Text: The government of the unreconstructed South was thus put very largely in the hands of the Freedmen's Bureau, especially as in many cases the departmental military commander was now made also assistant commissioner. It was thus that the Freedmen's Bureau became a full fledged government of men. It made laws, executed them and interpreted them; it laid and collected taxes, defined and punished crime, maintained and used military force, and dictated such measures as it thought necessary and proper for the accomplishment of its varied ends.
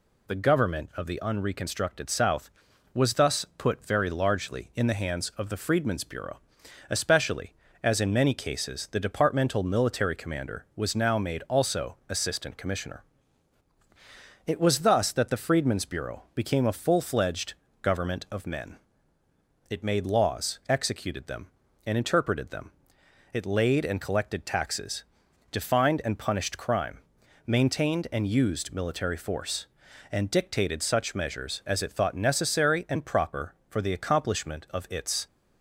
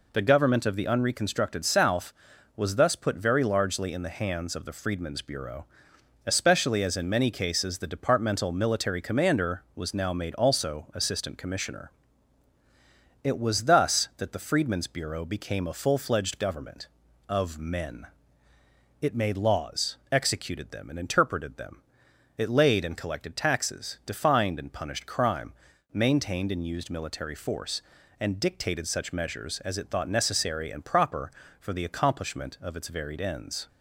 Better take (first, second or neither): second